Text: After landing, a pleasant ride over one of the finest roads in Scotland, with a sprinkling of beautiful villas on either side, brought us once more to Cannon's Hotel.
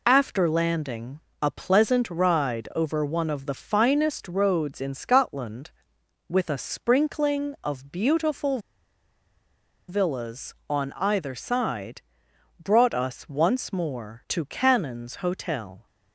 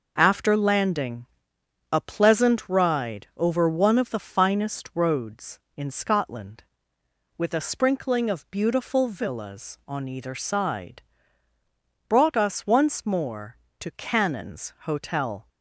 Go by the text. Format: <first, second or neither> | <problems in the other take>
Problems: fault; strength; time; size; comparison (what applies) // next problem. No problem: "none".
second | pauses between "beautiful" and "villas"; strong; at 8.5 s; 1.3 s long